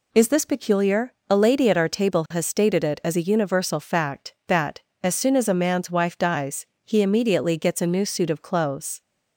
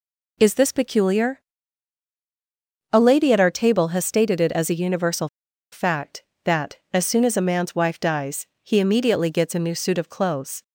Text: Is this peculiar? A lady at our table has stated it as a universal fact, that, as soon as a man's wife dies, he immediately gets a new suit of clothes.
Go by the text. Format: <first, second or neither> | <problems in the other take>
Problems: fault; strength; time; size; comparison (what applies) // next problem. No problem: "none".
first | pauses between "universal" and "fact"; at 5.2 s; 0.44 s long